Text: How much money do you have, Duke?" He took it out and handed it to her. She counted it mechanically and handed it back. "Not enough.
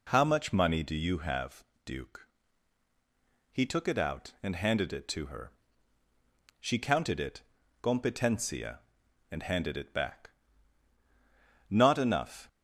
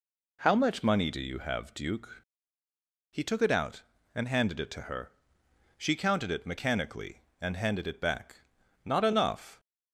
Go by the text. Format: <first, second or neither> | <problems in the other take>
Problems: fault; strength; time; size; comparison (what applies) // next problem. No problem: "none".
second | says "competencia" for "mechanically"; at 7.8 s